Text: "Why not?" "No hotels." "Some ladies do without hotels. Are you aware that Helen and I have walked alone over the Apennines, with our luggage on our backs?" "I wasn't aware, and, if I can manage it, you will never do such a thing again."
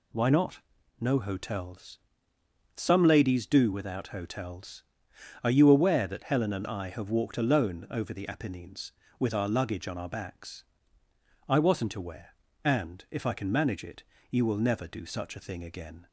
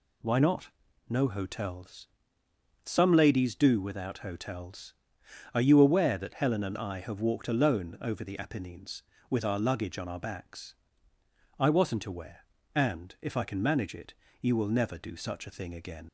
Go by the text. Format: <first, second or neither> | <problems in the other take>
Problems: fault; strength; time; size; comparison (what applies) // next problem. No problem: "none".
first | leaves "again" unfinished; at 16.0 s; 90 ms